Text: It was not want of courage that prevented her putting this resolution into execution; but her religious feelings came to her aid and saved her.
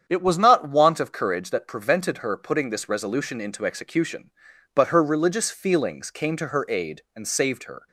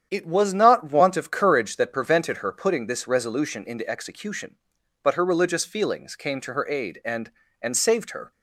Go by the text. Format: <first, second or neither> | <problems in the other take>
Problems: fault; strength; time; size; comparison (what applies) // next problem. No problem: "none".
first | starts louder than the rest; strong; until 1.1 s; 8.5 dB; strong in the first // says "and" twice; at 7.5 s